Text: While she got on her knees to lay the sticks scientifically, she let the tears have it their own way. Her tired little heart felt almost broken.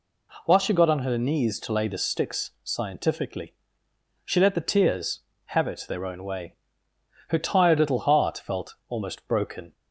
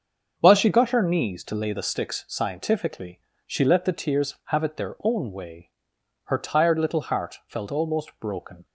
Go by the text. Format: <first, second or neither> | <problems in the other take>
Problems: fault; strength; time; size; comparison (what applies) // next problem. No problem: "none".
first | starts louder than the rest; until 1.3 s; 6.5 dB // skips "on"; at 0.9 s